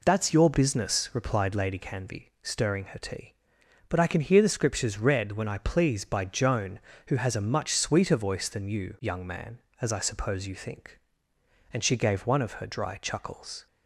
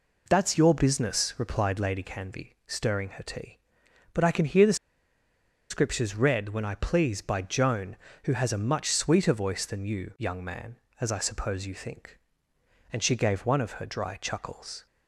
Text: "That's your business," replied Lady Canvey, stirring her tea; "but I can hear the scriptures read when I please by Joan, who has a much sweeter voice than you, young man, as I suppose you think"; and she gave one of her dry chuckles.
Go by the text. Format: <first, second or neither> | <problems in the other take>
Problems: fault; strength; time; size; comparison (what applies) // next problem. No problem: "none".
first | pauses between "the" and "scriptures"; noticeable; at 4.7 s; 0.95 s long